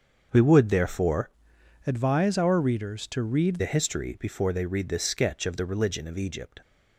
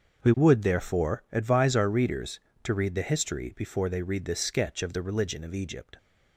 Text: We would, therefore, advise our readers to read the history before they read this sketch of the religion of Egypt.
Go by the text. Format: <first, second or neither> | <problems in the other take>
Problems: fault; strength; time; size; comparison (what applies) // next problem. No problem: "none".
second | starts louder than the rest; until 1.3 s; 6.5 dB; also in the second // changes voice from "advise" to "read"; from 1.8 to 3.6 s; 1.8 s long